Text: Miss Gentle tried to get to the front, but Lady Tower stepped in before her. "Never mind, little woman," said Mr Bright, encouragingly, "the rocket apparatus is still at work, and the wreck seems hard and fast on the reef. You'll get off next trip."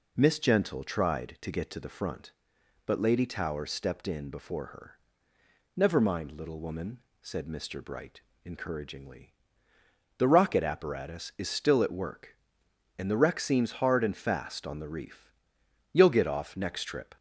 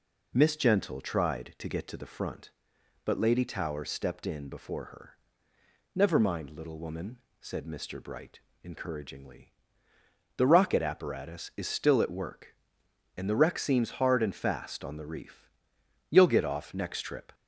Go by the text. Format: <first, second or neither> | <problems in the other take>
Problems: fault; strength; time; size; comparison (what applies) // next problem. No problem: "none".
neither | none